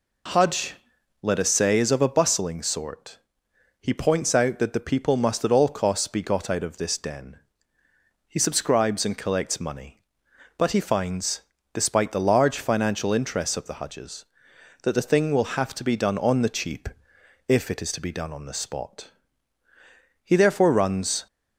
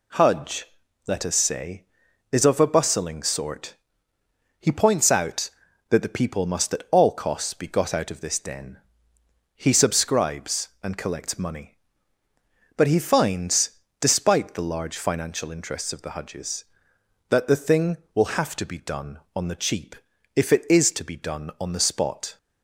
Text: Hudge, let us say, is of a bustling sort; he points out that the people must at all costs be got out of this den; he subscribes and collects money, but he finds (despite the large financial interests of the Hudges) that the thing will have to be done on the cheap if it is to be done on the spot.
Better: second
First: pauses between "cheap" and "if"; noticeable; at 16.8 s; 0.58 s long // goes on to say "He therefore runs"; noticeable; from 20.2 s on; 1.0 s long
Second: pauses between "cheap" and "if"; at 19.9 s; 0.40 s long

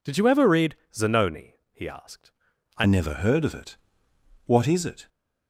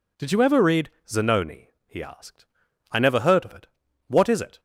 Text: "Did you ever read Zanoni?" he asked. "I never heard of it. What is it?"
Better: second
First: pauses between "read" and "Zanoni"; slight; at 0.7 s; 0.18 s long // changes voice at "never"; from 2.8 s on; 2.2 s long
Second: pauses between "read" and "Zanoni"; slight; at 0.9 s; 0.18 s long

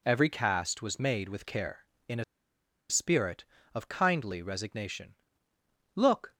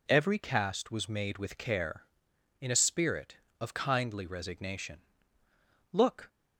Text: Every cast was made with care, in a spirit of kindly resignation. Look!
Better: second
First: pauses between "a" and "spirit"; noticeable; at 2.2 s; 0.66 s long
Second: none

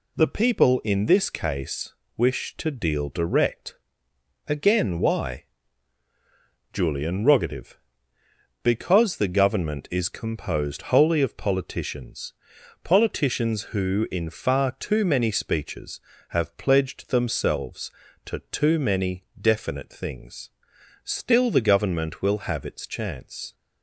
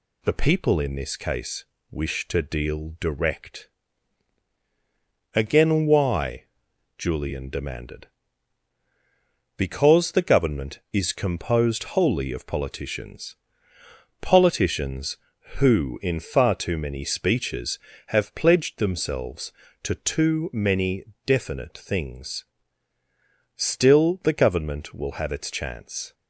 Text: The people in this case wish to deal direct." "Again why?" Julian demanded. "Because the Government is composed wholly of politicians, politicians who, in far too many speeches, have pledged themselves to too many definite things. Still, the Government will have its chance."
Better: second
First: pauses between "case" and "wish"; slight; at 1.9 s; 0.22 s long // says "rogative" for "demanded"; at 7.2 s // pauses between "many" and "definite"; slight; at 19.2 s; 0.18 s long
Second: pauses between "case" and "wish"; slight; at 1.6 s; 0.26 s long // pauses between "many" and "definite"; slight; at 21.0 s; 0.22 s long

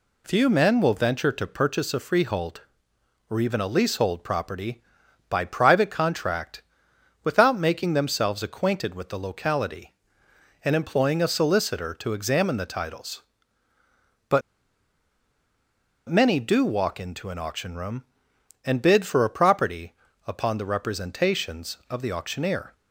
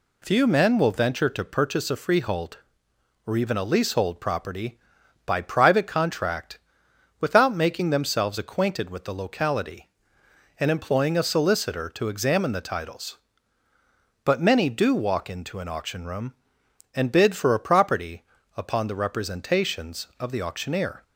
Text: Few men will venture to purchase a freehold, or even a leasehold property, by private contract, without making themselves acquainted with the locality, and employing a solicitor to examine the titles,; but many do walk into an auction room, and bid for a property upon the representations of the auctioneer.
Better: second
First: pauses between "but" and "many"; strong; at 14.4 s; 1.6 s long // pauses between "property" and "upon"; slight; at 19.9 s; 0.34 s long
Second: pauses between "property" and "upon"; slight; at 18.2 s; 0.34 s long

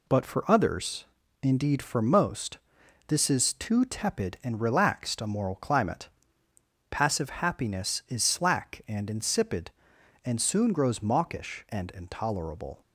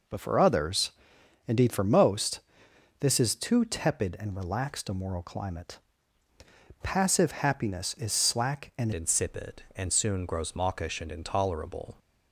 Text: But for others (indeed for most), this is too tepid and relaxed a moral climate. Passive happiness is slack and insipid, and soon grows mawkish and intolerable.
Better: first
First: none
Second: changes voice at "insipid"; from 8.9 s on; 3.0 s long

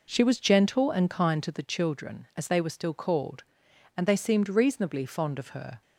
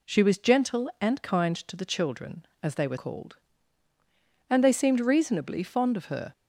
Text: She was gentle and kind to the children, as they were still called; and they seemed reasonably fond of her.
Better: first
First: none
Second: skips "still"; at 2.9 s

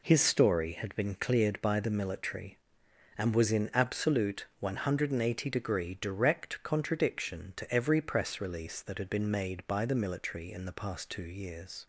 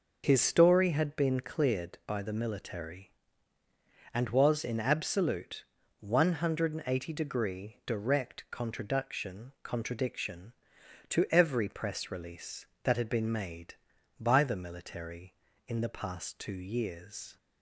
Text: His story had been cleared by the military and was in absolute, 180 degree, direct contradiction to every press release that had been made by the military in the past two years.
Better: first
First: none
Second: says "contradiction" twice; at 9.6 s

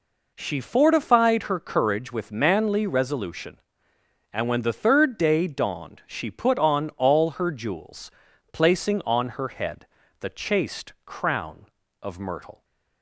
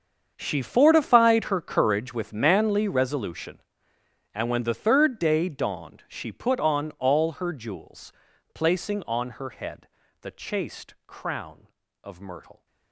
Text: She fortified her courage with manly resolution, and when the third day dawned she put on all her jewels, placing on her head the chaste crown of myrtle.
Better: first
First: pauses between "head" and "the"; slight; at 9.8 s; 0.32 s long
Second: gets quieter; strong; throughout; 17 dB // pauses between "head" and "the"; slight; at 9.8 s; 0.32 s long

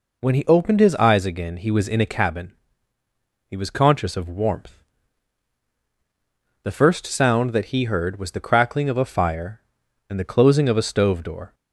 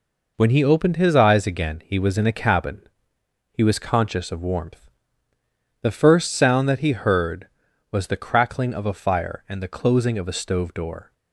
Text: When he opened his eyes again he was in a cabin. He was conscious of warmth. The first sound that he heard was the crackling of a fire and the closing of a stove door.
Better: neither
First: none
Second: none

